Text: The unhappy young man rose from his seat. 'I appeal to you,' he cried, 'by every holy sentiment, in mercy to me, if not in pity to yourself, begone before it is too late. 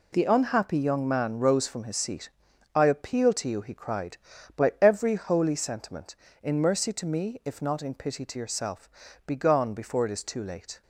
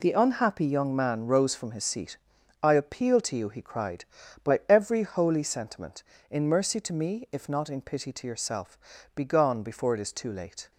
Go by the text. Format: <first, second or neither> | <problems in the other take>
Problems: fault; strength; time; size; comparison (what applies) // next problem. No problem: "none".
neither | none